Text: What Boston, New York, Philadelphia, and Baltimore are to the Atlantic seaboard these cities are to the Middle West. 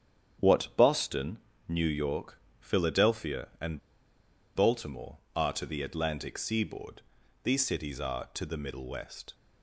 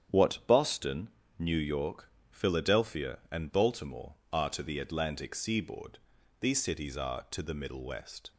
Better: second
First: starts louder than the rest; strong; until 1.8 s; 9 dB // pauses between "and" and "Baltimore"; noticeable; at 3.7 s; 0.77 s long // pauses between "seaboard" and "these"; at 7.0 s; 0.42 s long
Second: starts louder than the rest; strong; until 1.4 s; 9 dB // pauses between "seaboard" and "these"; at 5.9 s; 0.42 s long

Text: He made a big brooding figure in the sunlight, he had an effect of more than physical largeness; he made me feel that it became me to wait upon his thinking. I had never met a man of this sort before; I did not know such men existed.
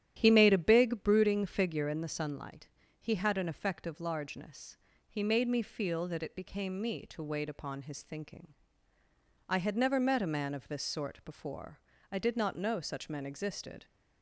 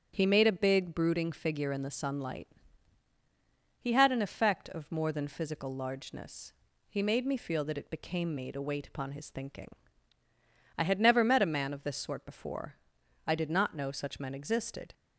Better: second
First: starts louder than the rest; strong; until 1.1 s; 11 dB // skips "more than physical"; at 4.0 s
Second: starts louder than the rest; strong; until 1.1 s; 8 dB

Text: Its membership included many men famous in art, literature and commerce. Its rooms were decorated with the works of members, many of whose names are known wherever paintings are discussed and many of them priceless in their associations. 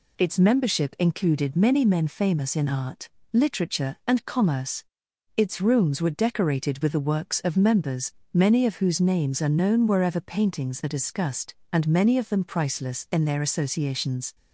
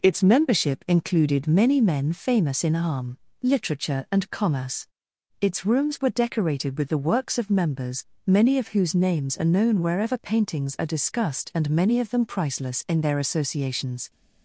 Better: first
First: none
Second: says "arm" for "art"; at 2.7 s

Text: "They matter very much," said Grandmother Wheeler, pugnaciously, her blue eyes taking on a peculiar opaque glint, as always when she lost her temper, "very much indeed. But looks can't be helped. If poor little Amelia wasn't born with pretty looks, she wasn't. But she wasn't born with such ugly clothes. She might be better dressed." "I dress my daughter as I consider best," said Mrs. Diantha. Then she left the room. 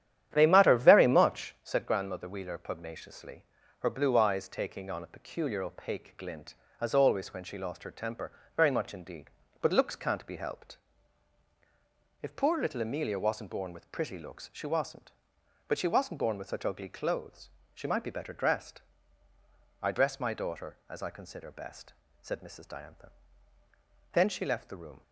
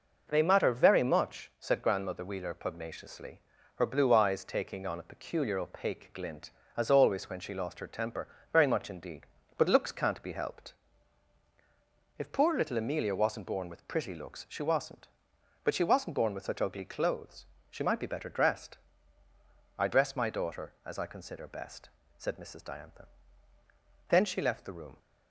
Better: second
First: starts louder than the rest; strong; until 1.7 s; 10.5 dB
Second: none

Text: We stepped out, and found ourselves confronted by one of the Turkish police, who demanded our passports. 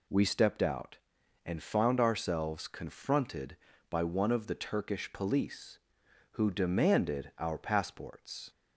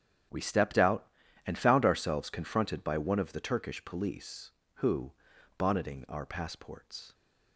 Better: first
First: none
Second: starts louder than the rest; strong; until 1.7 s; 10 dB // says "bonneting" for "demanded"; at 5.5 s

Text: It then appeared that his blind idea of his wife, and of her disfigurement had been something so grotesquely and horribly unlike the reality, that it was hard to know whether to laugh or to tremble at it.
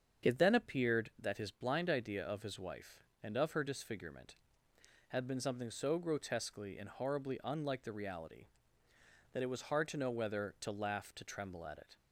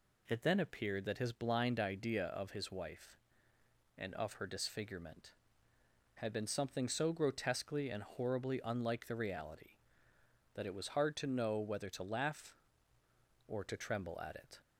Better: second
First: starts louder than the rest; strong; until 1.3 s; 7.5 dB // skips "or"; at 11.1 s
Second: none

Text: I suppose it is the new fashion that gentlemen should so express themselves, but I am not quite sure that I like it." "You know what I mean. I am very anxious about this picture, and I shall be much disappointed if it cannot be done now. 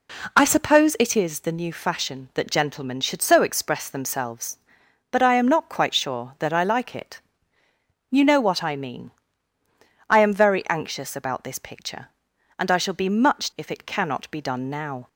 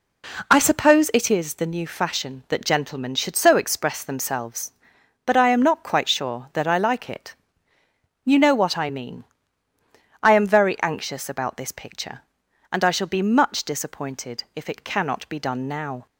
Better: second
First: skips "disappointed"; at 13.5 s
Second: none

